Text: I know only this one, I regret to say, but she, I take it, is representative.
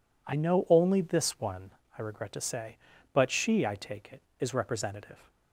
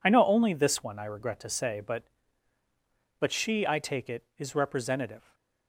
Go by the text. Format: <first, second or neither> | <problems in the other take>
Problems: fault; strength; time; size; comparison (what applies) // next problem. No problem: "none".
first | says "but" twice; at 3.1 s